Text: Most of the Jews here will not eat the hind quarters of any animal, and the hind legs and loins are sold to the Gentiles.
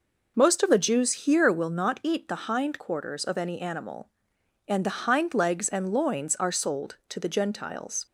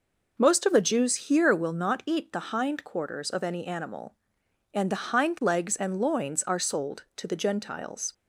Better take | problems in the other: neither | none

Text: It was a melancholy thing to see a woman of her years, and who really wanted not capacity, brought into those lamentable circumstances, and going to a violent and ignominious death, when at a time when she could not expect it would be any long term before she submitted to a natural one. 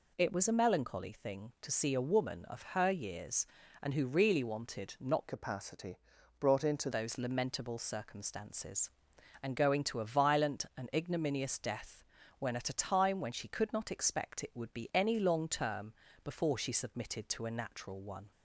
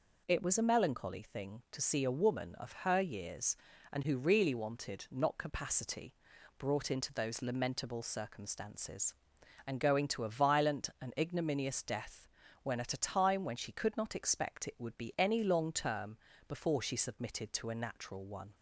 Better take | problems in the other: second | changes voice from "capacity" to "into"; from 5.2 to 6.8 s; 1.6 s long // pauses between "term" and "before"; slight; at 15.9 s; 0.32 s long; slight in the second

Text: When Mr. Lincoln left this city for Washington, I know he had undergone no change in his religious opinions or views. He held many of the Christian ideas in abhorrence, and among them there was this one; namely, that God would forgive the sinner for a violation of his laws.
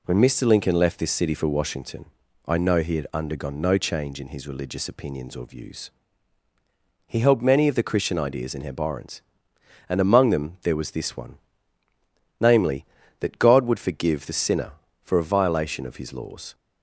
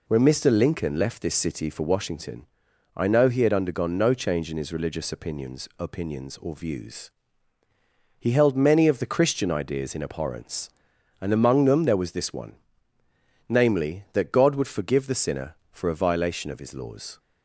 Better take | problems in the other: first | says "opinions" twice; at 5.7 s

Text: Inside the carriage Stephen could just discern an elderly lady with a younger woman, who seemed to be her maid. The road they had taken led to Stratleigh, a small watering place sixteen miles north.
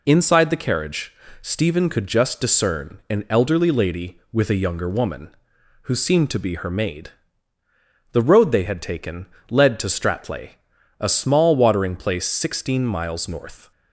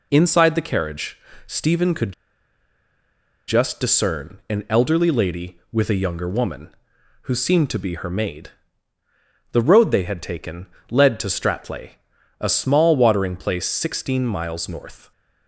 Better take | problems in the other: first | pauses between "carriage" and "Stephen"; slight; at 1.1 s; 0.30 s long; slight in the first // pauses between "could" and "just"; strong; at 2.1 s; 1.3 s long // pauses between "taken" and "led"; slight; at 10.6 s; 0.24 s long; slight in the first

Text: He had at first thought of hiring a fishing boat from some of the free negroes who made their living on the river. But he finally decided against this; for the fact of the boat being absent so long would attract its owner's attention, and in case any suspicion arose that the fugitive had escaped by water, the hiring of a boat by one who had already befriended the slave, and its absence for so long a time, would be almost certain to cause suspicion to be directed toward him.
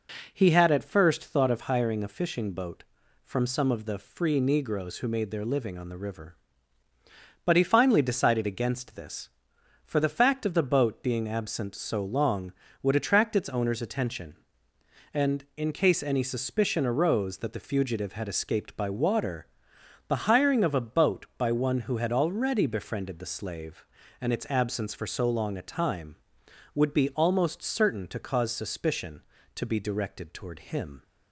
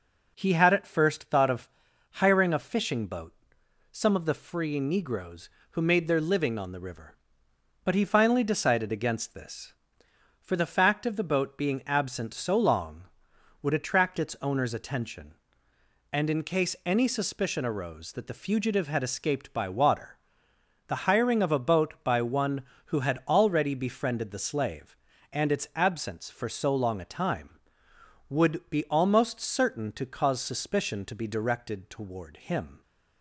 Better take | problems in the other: first | pauses between "of" and "hiring"; at 1.6 s; 0.42 s long // skips "from"; at 3.6 s

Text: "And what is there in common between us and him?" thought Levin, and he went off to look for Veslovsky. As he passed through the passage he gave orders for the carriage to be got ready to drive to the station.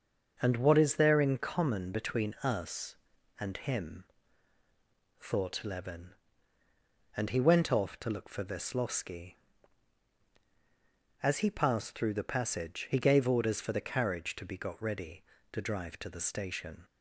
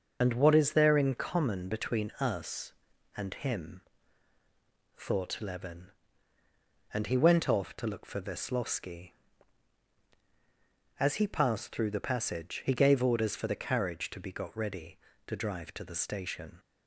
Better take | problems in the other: first | loses the start of "And"; at 0.2 s; 45 ms // starts louder than the rest; until 1.2 s; 6.5 dB; also in the first

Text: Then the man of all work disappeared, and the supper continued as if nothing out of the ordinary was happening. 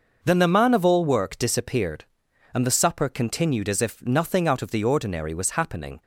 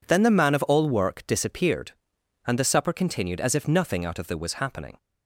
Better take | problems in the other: first | skips "ordinary"; at 4.3 s

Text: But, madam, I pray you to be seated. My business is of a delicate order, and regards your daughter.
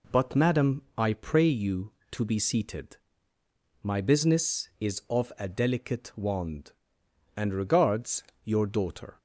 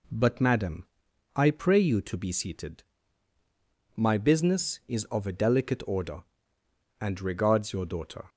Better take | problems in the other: second | says "wand" for "order"; at 6.1 s // pauses between "regards" and "your"; slight; at 8.2 s; 0.20 s long

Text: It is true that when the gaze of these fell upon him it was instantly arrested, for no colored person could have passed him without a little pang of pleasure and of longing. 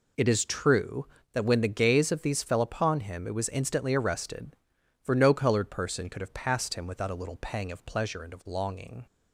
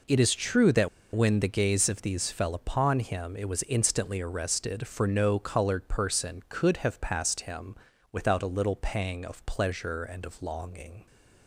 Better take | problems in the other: first | pauses between "that" and "when"; slight; at 0.8 s; 0.27 s long // pauses between "him" and "without"; slight; at 7.7 s; 0.36 s long

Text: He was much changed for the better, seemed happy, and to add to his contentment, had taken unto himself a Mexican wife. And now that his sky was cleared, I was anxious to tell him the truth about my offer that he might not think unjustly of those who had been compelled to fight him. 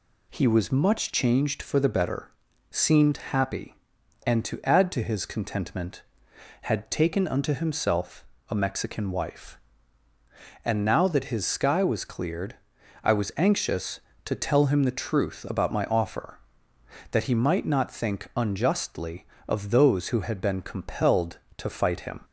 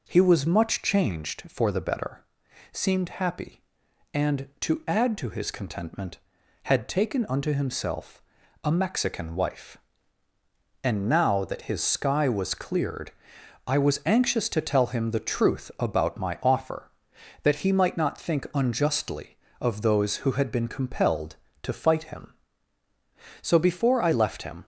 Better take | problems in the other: first | pauses between "himself" and "a"; at 8.2 s; 0.40 s long; slight in the first // goes on to say "So before I left him"; noticeable; from 23.4 s on; 1.2 s long

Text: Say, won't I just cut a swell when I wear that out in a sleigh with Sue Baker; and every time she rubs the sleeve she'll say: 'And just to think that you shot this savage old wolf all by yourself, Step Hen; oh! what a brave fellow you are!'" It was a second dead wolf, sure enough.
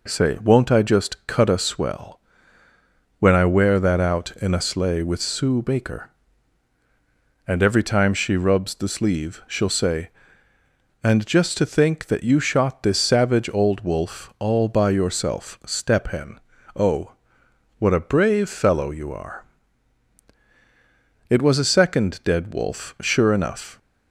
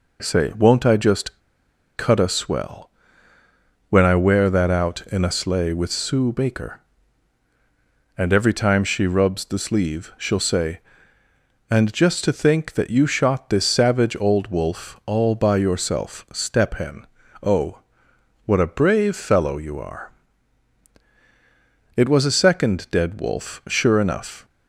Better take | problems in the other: first | pauses between "just" and "cut"; noticeable; at 1.4 s; 0.56 s long // pauses between "swell" and "when"; noticeable; at 2.9 s; 0.98 s long; noticeable in the first

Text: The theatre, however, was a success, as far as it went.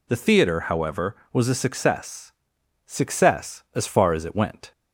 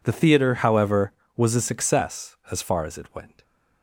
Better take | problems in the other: second | says "success" twice; at 2.8 s

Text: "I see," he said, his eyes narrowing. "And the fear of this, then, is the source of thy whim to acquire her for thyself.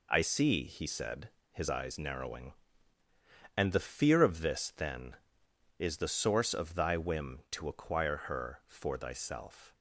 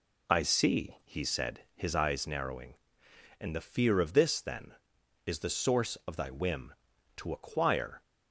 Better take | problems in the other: first | stops before "her for thyself"; at 8.0 s

